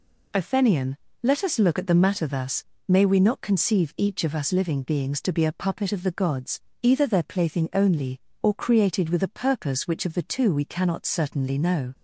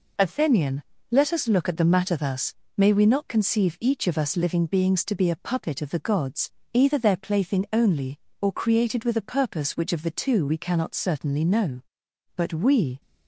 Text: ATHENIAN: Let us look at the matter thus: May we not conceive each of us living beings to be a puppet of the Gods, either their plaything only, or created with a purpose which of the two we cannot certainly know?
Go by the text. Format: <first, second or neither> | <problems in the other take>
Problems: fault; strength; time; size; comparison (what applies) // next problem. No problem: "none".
first | goes on to say "But we"; noticeable; from 12.3 s on; 0.64 s long